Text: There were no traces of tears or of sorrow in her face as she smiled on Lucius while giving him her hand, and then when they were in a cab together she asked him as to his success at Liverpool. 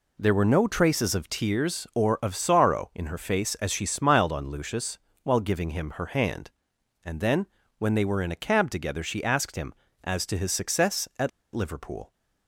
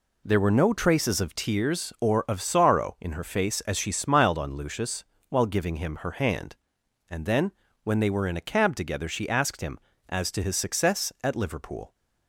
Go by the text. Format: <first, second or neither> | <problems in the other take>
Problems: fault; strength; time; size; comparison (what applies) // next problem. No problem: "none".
second | pauses between "Lucius" and "while"; slight; at 4.9 s; 0.24 s long; slight in the second // pauses between "then" and "when"; slight; at 7.4 s; 0.32 s long; slight in the second // pauses between "at" and "Liverpool"; slight; at 11.2 s; 0.24 s long